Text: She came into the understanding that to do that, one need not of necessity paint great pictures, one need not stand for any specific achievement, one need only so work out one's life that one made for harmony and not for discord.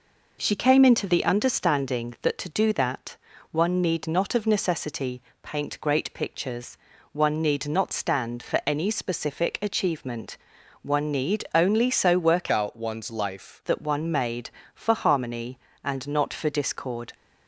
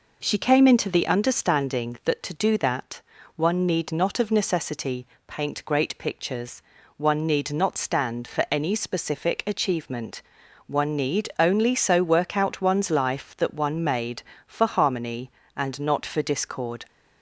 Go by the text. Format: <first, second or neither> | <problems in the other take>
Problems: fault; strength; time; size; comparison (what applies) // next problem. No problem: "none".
second | pauses between "necessity" and "paint"; slight; at 5.2 s; 0.20 s long; slight in the second // changes voice from "out" to "life"; from 12.5 to 13.6 s; 1.1 s long